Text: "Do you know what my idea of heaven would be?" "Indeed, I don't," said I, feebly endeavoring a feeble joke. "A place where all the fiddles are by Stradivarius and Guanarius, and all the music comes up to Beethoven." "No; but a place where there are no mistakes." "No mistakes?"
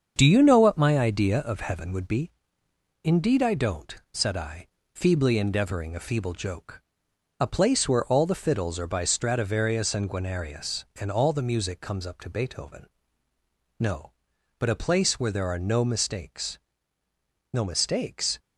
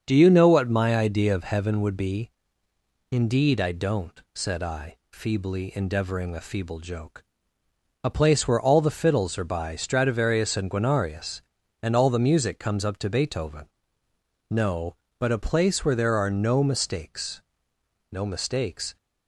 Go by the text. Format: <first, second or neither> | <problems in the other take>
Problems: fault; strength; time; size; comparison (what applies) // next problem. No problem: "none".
second | gets quieter; noticeable; throughout; 6 dB // starts louder than the rest; until 1.1 s; 7 dB; also in the second